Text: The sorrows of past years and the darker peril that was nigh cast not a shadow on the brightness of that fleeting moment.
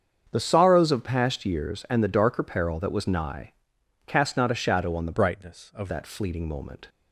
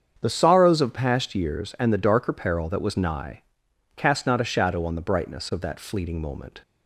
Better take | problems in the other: second | starts louder than the rest; strong; until 1.3 s; 7.5 dB; strong in the second // pauses between "nigh" and "cast"; noticeable; at 3.5 s; 0.52 s long; noticeable in the second // changes voice from "brightness" to "of"; from 5.1 to 5.8 s; 0.7 s long

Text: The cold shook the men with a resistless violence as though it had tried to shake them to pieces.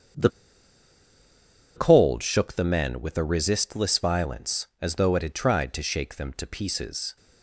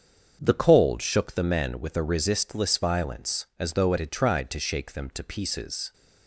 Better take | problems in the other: second | starts louder than the rest; strong; until 2.6 s; 7 dB; strong in the second // pauses between "The" and "cold"; strong; at 0.2 s; 1.4 s long

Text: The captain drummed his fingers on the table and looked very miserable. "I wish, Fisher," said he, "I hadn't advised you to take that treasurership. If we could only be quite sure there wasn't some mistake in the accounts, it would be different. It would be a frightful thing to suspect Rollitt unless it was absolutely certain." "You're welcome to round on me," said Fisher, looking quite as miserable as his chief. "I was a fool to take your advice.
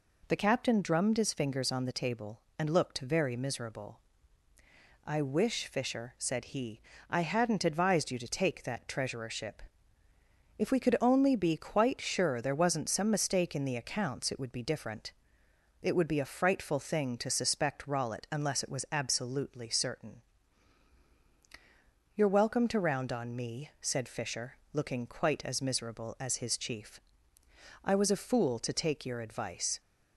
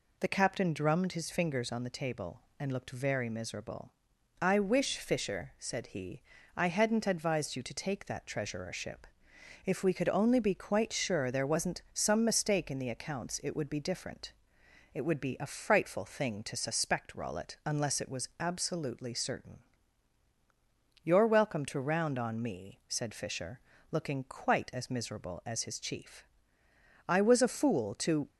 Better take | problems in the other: first | stops before "take your advice"; at 28.2 s

